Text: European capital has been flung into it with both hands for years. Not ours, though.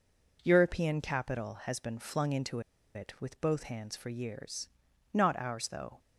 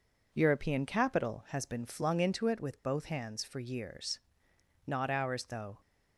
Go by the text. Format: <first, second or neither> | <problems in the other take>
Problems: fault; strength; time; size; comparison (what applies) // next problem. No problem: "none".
second | pauses between "into" and "it"; slight; at 2.6 s; 0.34 s long